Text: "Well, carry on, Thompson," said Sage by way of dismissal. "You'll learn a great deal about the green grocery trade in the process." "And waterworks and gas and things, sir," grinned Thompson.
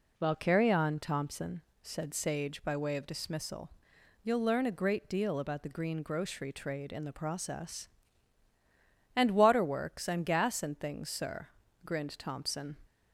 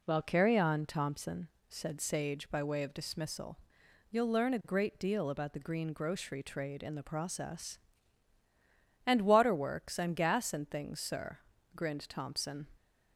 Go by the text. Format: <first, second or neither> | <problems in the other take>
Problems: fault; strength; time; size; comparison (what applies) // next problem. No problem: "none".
neither | none